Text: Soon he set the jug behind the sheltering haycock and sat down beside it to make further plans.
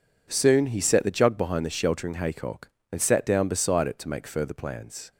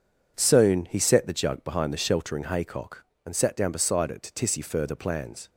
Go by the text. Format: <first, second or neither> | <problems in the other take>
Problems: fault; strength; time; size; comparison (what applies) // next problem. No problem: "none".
first | says "tissy" for "make"; at 4.4 s